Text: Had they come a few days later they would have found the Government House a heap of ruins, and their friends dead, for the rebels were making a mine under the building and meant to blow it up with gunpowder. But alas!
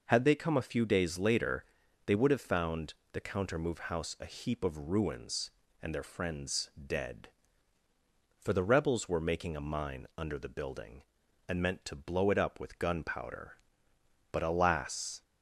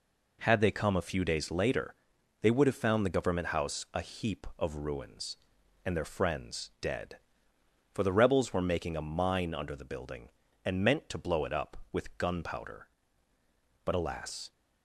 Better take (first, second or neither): second